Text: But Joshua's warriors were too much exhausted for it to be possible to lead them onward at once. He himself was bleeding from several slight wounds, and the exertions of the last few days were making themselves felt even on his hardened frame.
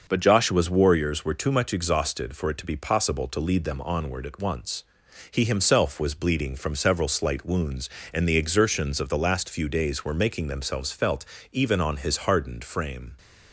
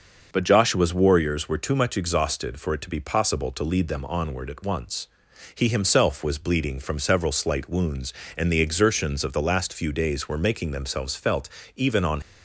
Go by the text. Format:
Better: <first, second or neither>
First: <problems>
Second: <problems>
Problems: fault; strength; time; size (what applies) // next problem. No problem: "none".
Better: first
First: pauses between "felt" and "even"; slight; at 11.2 s; 0.26 s long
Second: pauses between "felt" and "even"; slight; at 11.4 s; 0.26 s long // stops before "his hardened frame"; at 12.2 s